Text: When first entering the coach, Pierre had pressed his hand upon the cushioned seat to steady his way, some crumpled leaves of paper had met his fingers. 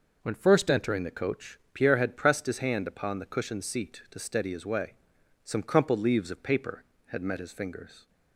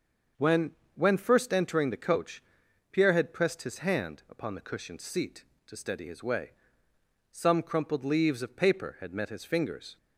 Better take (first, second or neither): first